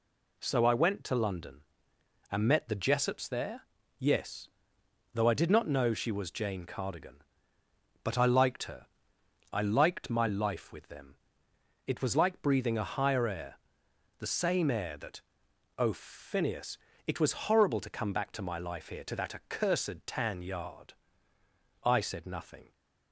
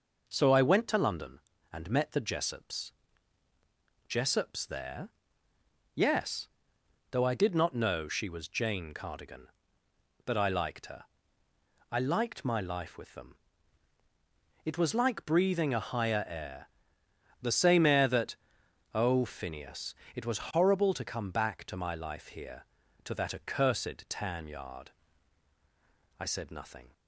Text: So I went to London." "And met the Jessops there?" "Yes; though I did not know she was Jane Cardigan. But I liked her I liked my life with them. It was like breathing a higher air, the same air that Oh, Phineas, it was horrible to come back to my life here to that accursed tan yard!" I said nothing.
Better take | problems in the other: first | says "Jessops" twice; at 4.0 s // pauses between "her" and "I"; noticeable; at 11.0 s; 0.88 s long; noticeable in the first // pauses between "that" and "Oh"; noticeable; at 18.3 s; 0.58 s long; noticeable in the first

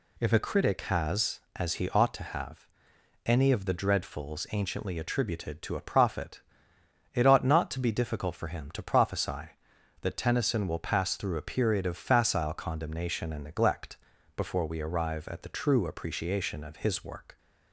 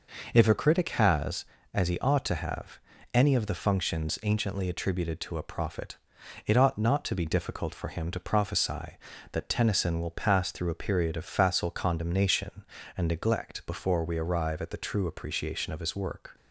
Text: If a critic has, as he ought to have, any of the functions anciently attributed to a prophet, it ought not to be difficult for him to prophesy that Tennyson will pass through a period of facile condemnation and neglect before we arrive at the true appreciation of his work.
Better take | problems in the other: second | says "dreadfuls" for "functions"; at 3.7 s // pauses between "neglect" and "before"; at 13.9 s; 0.40 s long

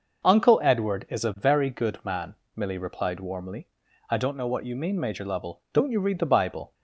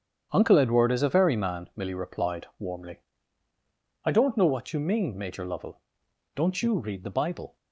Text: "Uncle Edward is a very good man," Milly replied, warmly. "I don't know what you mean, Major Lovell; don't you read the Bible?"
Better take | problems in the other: first | starts louder than the rest; strong; until 1.3 s; 8.5 dB; noticeable in the first // skips "good"; at 1.3 s

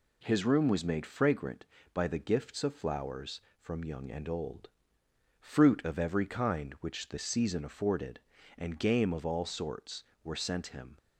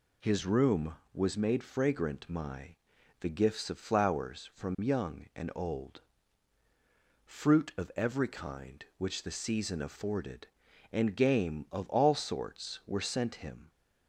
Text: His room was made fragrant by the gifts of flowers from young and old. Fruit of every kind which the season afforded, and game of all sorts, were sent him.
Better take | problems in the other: first | says "my" for "by"; at 2.2 s

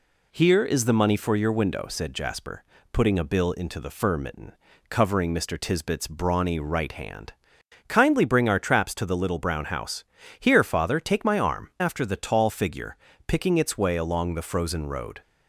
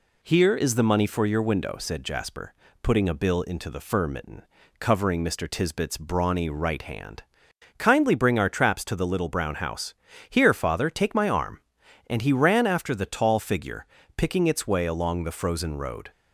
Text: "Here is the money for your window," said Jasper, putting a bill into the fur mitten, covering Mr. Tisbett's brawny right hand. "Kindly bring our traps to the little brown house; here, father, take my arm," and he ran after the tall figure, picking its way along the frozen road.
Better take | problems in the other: second | skips "and he ran"; at 11.7 s

